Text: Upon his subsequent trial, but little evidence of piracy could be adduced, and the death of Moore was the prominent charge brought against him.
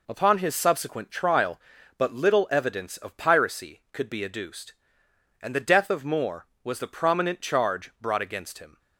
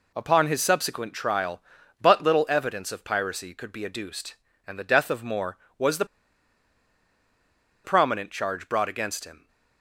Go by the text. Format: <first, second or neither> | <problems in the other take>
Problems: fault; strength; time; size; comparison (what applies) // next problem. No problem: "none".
first | pauses between "the" and "prominent"; strong; at 6.0 s; 1.7 s long